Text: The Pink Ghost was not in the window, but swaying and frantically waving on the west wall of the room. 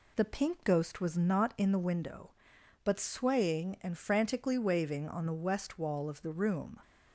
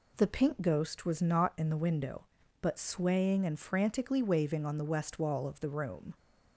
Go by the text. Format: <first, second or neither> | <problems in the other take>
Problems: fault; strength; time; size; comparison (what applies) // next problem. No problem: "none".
neither | none